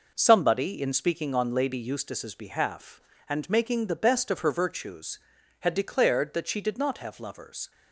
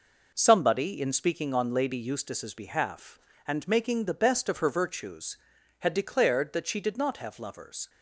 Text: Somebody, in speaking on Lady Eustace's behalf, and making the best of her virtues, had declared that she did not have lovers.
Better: neither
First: none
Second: none

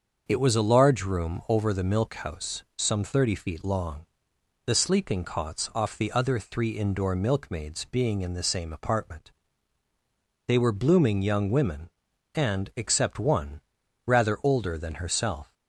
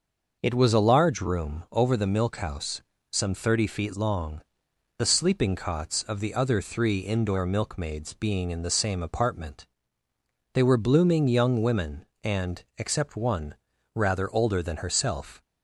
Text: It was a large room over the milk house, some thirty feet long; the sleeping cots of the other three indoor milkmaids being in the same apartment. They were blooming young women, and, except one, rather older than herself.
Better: second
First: starts louder than the rest; until 1.2 s; 6.5 dB // says "off" for "of"; at 5.7 s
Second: none

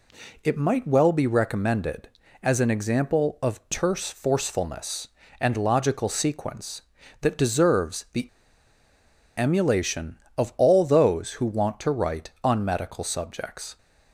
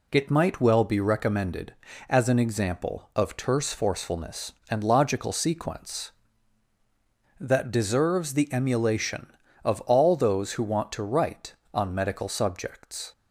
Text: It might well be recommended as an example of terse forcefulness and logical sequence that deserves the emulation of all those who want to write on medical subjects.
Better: second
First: pauses between "the" and "emulation"; at 8.2 s; 1.1 s long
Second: none

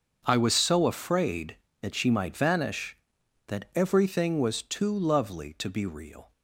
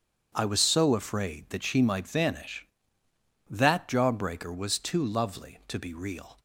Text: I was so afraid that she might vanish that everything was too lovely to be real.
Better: first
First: starts louder than the rest; until 1.2 s; 6.5 dB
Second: starts louder than the rest; strong; until 1.3 s; 8 dB // says "jawbreaker" for "everything"; at 3.8 s

